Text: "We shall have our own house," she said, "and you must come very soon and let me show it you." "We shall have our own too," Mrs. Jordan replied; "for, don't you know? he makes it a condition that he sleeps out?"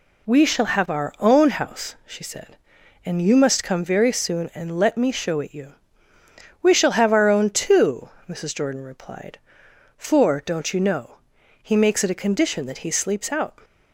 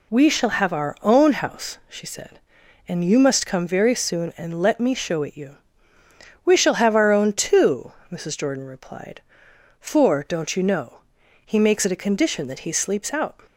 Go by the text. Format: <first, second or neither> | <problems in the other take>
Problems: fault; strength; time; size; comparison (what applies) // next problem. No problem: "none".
neither | none